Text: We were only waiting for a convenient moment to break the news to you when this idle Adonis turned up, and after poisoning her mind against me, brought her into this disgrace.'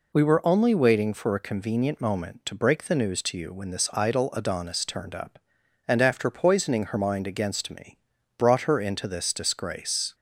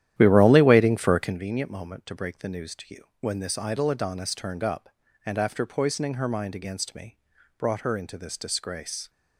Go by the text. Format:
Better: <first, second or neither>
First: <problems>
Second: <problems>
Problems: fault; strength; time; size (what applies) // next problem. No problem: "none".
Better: first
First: none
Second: starts louder than the rest; strong; until 1.4 s; 11.5 dB